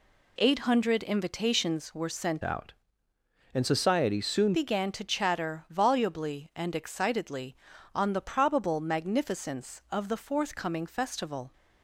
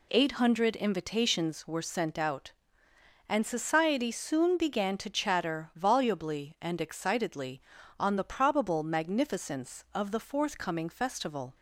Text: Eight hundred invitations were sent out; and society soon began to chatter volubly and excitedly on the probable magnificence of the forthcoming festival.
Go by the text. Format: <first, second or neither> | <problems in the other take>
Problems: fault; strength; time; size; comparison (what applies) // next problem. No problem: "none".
second | changes voice from "out" to "soon"; from 2.4 to 4.5 s; 2.1 s long